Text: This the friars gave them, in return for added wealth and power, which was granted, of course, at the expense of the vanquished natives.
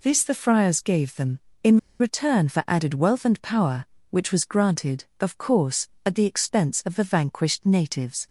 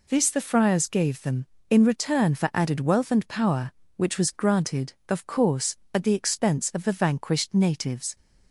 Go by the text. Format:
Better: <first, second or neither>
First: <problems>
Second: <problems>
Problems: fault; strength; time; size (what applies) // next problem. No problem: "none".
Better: second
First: pauses between "in" and "return"; slight; at 1.7 s; 0.21 s long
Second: none